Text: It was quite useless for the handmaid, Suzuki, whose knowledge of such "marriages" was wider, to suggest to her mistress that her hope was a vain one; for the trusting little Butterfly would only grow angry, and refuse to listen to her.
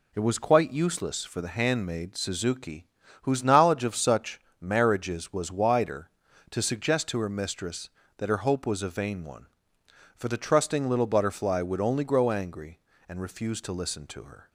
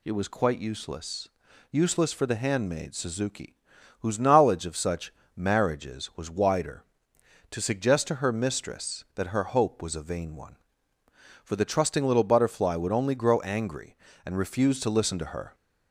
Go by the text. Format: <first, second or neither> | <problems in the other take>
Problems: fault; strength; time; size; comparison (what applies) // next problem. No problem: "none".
first | says "useless" twice; at 1.7 s // pauses between "such" and "marriages"; slight; at 5.1 s; 0.24 s long; slight in the first